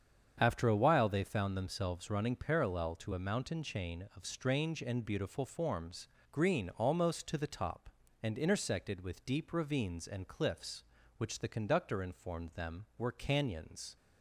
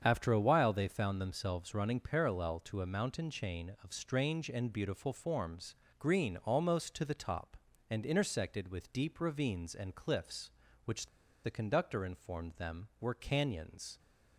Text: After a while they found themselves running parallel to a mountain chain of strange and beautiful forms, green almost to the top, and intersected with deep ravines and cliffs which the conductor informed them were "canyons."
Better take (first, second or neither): first